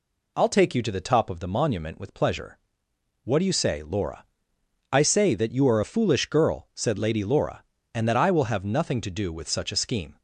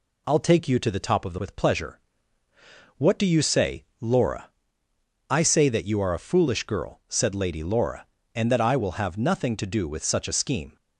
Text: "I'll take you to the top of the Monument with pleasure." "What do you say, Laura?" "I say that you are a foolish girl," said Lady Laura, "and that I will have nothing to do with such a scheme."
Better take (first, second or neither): first